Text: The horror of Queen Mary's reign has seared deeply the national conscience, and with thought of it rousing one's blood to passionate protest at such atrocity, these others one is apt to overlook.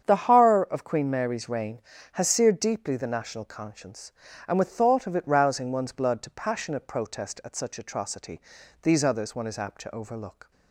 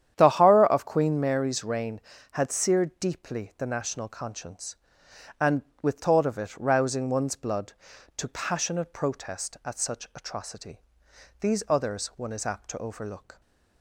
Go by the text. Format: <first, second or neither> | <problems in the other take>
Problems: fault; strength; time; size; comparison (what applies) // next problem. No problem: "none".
first | starts louder than the rest; strong; until 1.1 s; 10 dB; strong in the first // says "had" for "has"; at 2.3 s